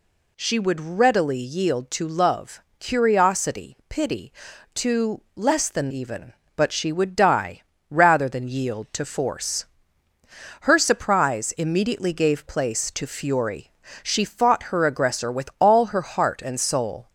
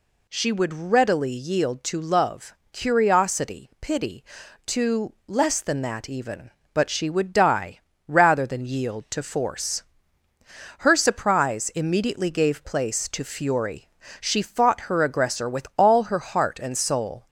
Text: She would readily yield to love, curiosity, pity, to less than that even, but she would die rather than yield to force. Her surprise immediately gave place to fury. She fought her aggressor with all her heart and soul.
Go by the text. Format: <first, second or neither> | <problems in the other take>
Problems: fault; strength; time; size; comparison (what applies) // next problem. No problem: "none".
second | skips "that"; at 5.9 s // pauses between "die" and "rather"; slight; at 7.6 s; 0.28 s long; slight in the second